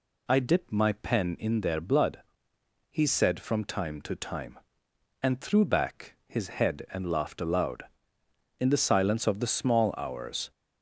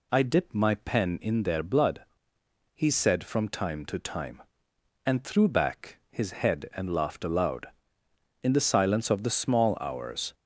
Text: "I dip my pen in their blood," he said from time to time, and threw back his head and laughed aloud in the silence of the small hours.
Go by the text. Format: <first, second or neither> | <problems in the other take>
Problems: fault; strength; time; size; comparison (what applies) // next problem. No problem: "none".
neither | none